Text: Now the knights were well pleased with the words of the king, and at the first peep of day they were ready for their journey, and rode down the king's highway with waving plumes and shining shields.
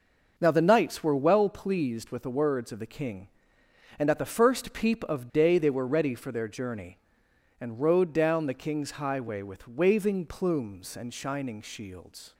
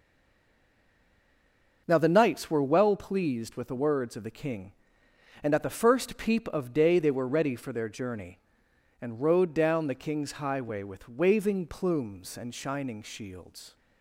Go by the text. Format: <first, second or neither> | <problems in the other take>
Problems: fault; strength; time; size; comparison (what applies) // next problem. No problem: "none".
first | stays silent before the first word; noticeable; until 1.8 s; 1.8 s long // starts louder than the rest; until 2.8 s; 6 dB; noticeable in the first